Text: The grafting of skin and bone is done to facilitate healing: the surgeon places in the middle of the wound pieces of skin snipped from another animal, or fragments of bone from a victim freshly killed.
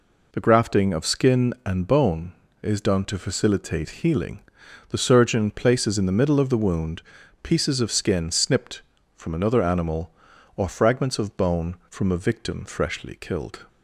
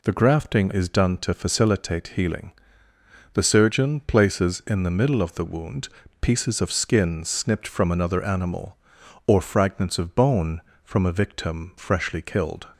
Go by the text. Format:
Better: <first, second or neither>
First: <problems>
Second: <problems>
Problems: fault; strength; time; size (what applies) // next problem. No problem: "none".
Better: first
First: pauses between "wound" and "pieces"; at 7.0 s; 0.40 s long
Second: skips "of skin and bone"; at 0.7 s // pauses between "wound" and "pieces"; slight; at 5.8 s; 0.32 s long